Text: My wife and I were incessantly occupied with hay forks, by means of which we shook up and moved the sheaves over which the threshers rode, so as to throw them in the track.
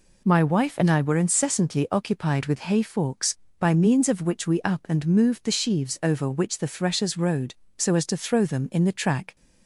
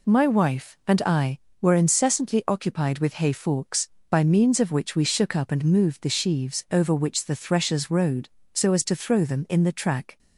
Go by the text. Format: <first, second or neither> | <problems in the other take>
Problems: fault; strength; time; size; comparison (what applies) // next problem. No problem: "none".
second | skips "shook"; at 4.6 s